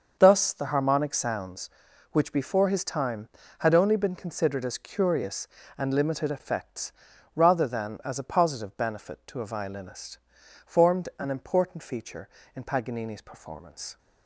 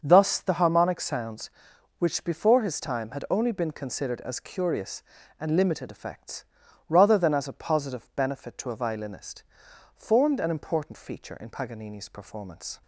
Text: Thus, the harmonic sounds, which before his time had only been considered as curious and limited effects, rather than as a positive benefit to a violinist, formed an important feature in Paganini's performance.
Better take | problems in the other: neither | starts louder than the rest; the same in both

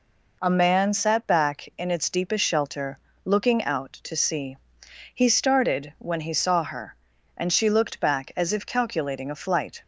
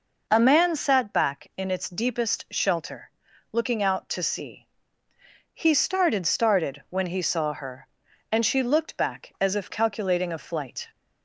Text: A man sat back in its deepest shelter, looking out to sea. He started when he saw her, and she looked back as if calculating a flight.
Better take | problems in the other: first | says "started" twice; at 6.2 s

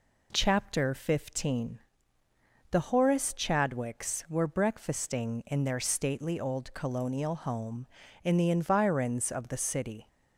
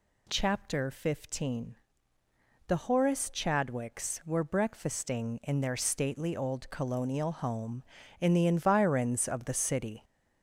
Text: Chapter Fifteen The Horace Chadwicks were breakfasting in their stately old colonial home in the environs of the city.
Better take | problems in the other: first | gets louder; noticeable; throughout; 4.5 dB // pauses between "Fifteen" and "The"; noticeable; at 1.7 s; 0.92 s long; noticeable in the first

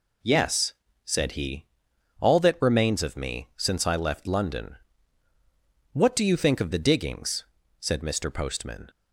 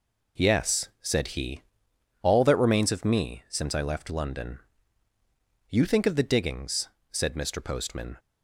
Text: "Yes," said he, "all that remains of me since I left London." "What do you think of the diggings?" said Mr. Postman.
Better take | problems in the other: first | skips "What do"; at 5.1 s

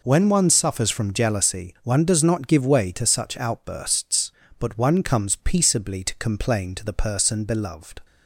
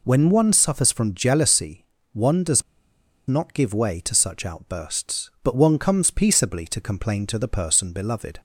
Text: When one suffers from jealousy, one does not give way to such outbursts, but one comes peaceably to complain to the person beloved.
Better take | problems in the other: first | pauses between "does" and "not"; noticeable; at 2.6 s; 0.65 s long

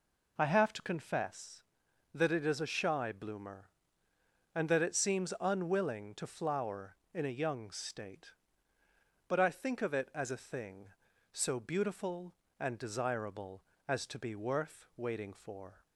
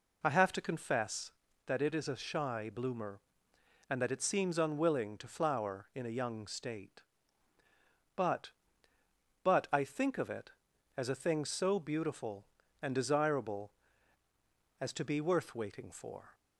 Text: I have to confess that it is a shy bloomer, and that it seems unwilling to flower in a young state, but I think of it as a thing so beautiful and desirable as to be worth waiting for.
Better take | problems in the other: first | says "but" twice; at 9.4 s

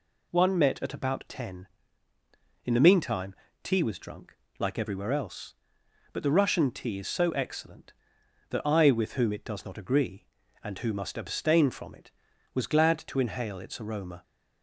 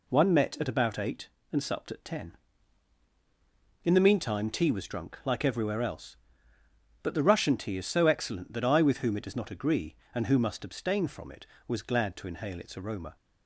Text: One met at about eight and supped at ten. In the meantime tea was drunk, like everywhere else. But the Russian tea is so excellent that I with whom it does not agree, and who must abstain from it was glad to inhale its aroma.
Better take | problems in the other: second | skips "eight and supped at"; at 1.2 s // pauses between "meantime" and "tea"; slight; at 3.3 s; 0.28 s long

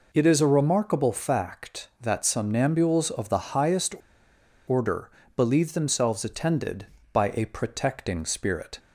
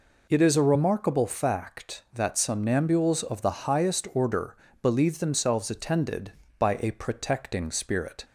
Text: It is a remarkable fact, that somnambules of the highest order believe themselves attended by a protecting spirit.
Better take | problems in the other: second | pauses between "highest" and "order"; noticeable; at 3.9 s; 0.74 s long // pauses between "order" and "believe"; slight; at 5.1 s; 0.24 s long; slight in the second

